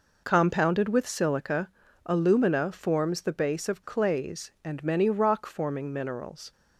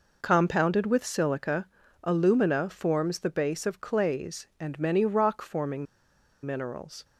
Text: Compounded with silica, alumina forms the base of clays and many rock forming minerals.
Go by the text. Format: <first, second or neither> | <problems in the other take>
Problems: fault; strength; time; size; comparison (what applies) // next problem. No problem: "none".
first | pauses between "forming" and "minerals"; noticeable; at 5.8 s; 0.58 s long